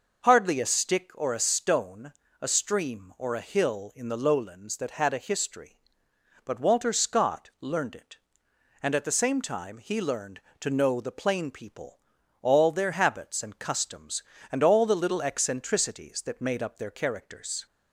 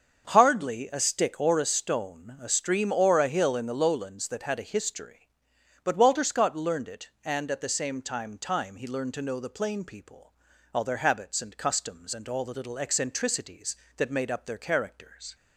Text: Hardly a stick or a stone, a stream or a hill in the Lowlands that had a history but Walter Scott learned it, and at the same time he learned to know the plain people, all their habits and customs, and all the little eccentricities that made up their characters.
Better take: first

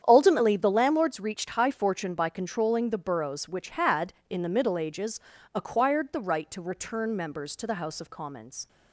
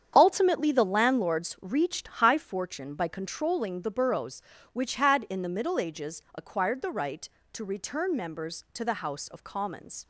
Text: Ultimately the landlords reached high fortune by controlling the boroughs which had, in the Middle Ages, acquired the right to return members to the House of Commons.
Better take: neither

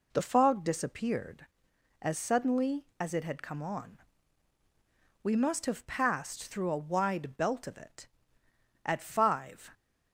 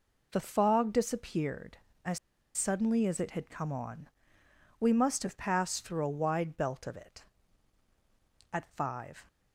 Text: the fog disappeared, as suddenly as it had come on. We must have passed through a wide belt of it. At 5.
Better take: first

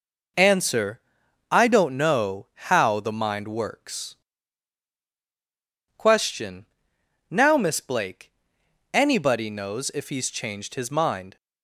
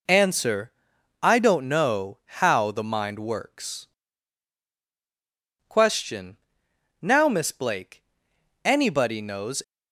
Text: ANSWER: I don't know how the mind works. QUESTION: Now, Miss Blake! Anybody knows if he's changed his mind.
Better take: first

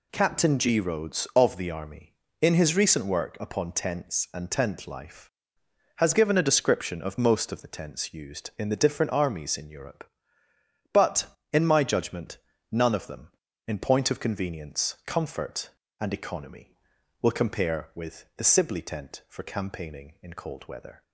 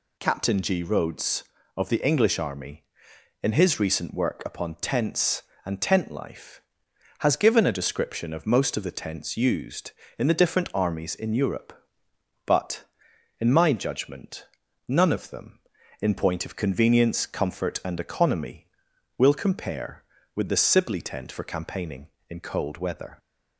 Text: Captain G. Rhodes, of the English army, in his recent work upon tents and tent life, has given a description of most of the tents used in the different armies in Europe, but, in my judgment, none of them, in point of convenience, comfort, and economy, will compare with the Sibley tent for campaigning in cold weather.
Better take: second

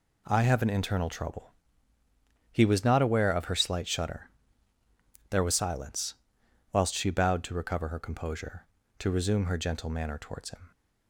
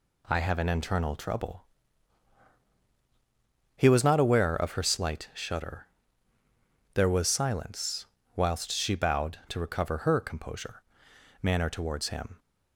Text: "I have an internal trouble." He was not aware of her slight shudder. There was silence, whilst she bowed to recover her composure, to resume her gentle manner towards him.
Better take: first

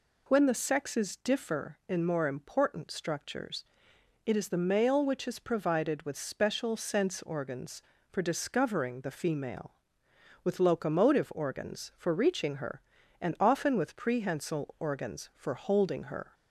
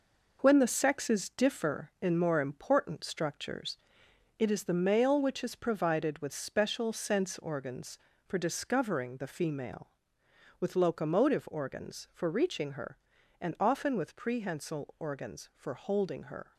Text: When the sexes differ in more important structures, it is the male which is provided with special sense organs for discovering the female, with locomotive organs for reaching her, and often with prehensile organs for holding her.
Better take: first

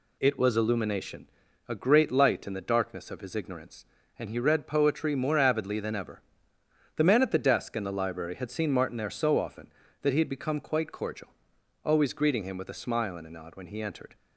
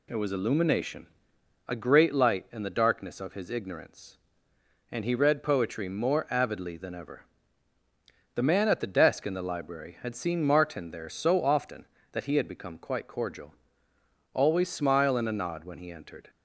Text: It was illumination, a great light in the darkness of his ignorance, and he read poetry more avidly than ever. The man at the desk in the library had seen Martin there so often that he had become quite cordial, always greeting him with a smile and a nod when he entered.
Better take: first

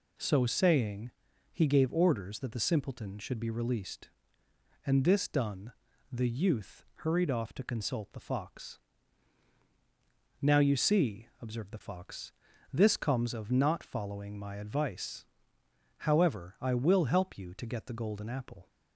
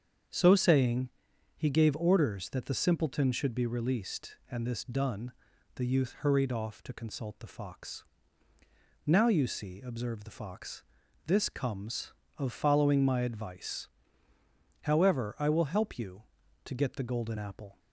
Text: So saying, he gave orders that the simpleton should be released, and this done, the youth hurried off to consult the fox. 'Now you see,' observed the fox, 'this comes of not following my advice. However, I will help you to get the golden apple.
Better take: first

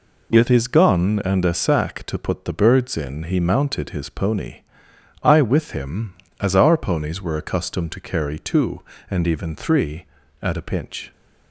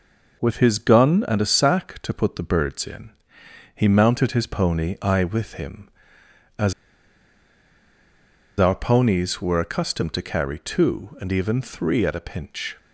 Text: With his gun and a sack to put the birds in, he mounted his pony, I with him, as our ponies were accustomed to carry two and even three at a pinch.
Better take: first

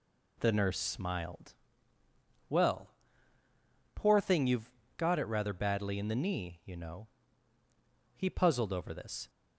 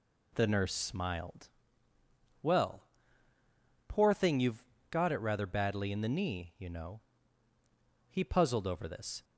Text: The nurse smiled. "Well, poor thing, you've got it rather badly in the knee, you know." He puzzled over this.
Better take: neither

